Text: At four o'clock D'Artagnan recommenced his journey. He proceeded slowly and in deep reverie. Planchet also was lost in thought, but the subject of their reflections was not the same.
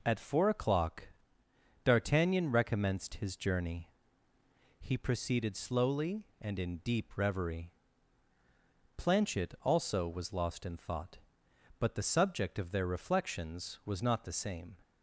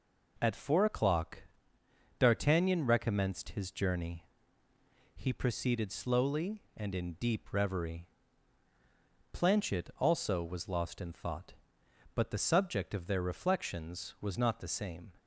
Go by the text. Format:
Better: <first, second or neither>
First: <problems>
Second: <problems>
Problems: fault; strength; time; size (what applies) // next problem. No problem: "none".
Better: neither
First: pauses between "o'clock" and "D'Artagnan"; noticeable; at 1.0 s; 0.74 s long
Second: pauses between "o'clock" and "D'Artagnan"; noticeable; at 1.4 s; 0.74 s long